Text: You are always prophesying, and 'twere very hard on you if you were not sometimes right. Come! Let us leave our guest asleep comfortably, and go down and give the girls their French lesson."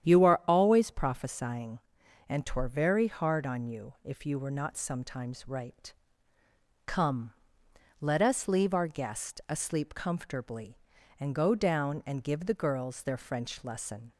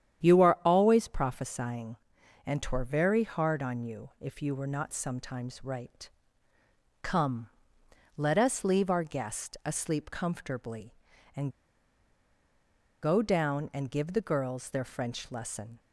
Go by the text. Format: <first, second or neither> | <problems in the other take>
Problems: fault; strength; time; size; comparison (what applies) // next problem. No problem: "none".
first | starts louder than the rest; strong; until 1.3 s; 9.5 dB; strong in the first // pauses between "and" and "go"; strong; at 11.4 s; 1.5 s long